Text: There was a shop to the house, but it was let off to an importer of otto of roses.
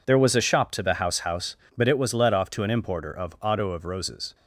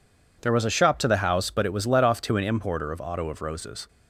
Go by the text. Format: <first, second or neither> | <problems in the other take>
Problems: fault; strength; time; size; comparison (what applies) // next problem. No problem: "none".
second | says "house" twice; at 1.1 s